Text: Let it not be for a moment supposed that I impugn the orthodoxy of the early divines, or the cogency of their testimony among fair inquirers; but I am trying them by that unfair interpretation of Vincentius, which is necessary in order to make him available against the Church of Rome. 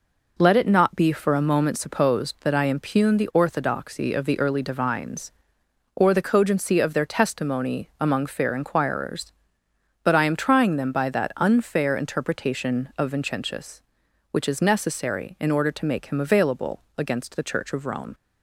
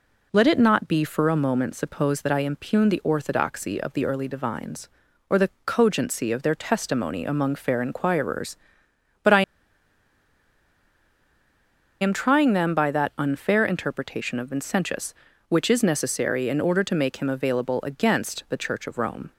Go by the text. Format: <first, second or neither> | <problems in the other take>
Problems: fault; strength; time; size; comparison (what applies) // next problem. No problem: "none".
first | pauses between "the" and "cogency"; slight; at 5.4 s; 0.16 s long // pauses between "I" and "am"; strong; at 9.4 s; 2.5 s long